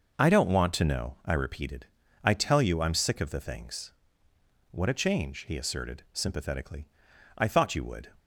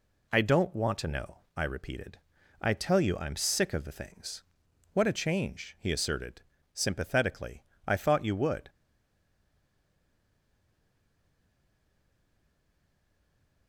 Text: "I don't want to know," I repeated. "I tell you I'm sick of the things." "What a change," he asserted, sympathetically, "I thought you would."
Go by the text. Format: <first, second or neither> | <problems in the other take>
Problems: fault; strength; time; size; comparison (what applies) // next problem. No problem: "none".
first | stays silent after the last word; strong; from 8.6 s on; 5.0 s long